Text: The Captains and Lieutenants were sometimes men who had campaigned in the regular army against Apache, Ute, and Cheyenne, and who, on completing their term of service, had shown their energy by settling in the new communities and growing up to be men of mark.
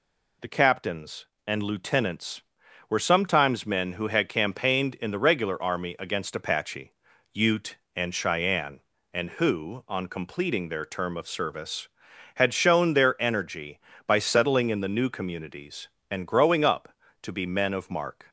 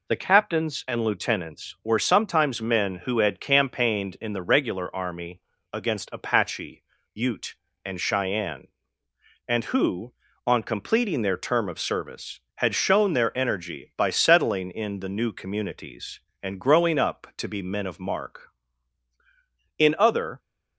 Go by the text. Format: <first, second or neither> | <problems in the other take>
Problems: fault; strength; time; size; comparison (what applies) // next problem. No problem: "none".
first | pauses between "army" and "against"; slight; at 5.4 s; 0.32 s long // goes on to say "In other"; noticeable; from 19.7 s on; 0.62 s long